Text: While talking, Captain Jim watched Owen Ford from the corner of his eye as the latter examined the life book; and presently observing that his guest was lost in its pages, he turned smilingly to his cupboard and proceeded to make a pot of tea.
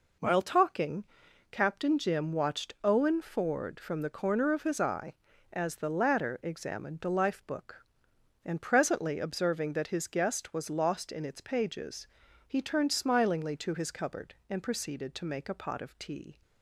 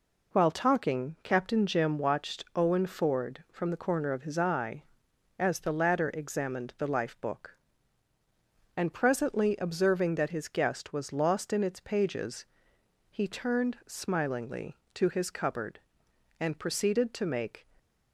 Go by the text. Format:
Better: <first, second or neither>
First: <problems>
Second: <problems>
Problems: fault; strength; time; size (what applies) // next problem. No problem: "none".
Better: first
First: none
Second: stops before "a pot of tea"; at 17.7 s